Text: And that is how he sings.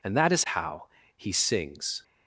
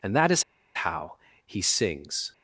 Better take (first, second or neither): first